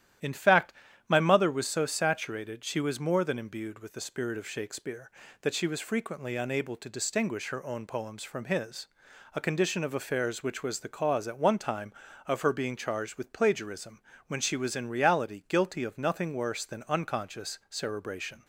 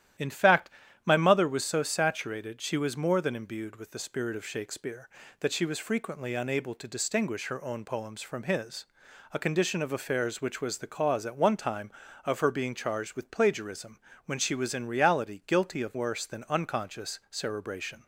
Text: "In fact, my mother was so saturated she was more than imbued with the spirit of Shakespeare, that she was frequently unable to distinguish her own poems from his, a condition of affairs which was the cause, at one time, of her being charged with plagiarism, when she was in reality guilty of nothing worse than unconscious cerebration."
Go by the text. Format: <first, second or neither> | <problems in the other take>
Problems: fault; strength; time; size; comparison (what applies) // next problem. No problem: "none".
first | starts louder than the rest; strong; until 1.5 s; 12 dB; strong in the first // skips "nothing"; at 15.9 s